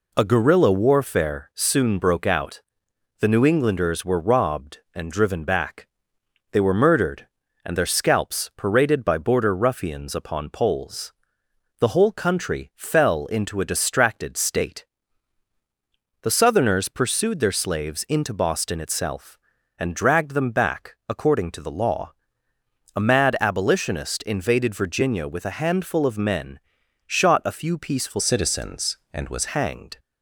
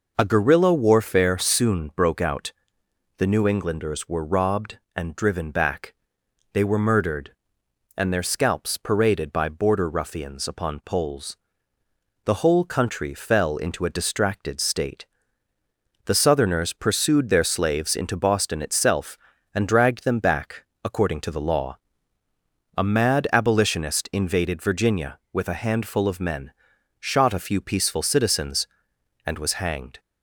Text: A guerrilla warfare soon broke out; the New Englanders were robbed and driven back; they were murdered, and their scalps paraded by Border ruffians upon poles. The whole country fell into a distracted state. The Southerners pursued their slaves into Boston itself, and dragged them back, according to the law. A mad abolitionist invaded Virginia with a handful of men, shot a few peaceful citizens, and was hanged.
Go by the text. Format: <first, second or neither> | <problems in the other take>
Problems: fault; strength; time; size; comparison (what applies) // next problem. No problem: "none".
second | changes voice from "citizens" to "was"; from 28.2 to 29.4 s; 1.2 s long